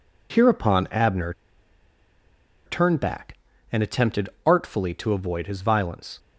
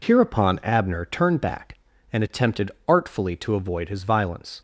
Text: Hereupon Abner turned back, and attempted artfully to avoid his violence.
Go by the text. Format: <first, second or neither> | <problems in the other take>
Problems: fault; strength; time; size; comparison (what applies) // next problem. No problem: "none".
second | pauses between "Abner" and "turned"; strong; at 1.3 s; 1.3 s long // pauses between "attempted" and "artfully"; slight; at 4.2 s; 0.16 s long; slight in the second